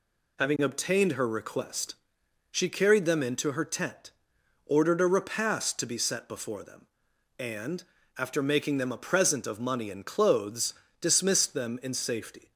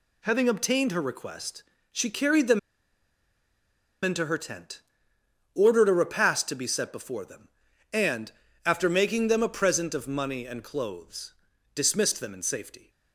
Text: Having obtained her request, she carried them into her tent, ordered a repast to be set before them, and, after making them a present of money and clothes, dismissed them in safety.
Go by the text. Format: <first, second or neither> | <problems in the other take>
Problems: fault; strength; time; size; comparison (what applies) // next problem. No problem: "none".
first | pauses between "them" and "into"; strong; at 2.5 s; 1.4 s long